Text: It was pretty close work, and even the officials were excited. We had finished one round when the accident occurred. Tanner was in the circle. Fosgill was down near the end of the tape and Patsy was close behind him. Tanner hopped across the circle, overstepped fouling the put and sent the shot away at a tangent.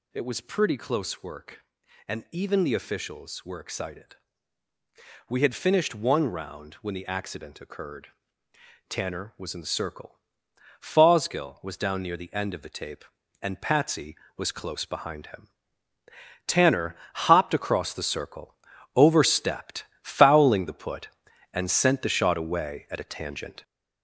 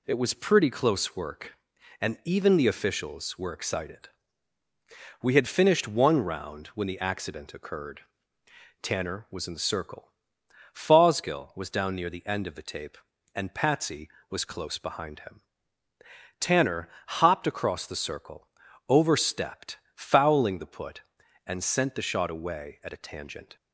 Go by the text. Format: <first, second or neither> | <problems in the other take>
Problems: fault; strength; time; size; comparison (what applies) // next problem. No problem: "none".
second | gets louder; throughout; 6 dB // pauses between "Tanner" and "hopped"; slight; at 16.9 s; 0.32 s long; slight in the second // pauses between "overstepped" and "fouling"; slight; at 19.8 s; 0.18 s long; slight in the second